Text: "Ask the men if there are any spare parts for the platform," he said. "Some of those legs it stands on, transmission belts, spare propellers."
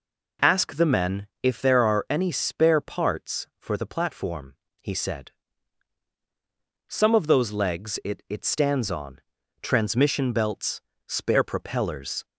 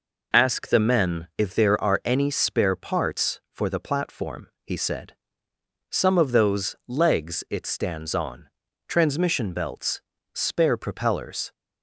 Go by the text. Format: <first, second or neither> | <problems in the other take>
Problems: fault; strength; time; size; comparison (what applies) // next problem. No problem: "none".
second | pauses between "men" and "if"; slight; at 1.2 s; 0.16 s long // says "it" twice; at 8.3 s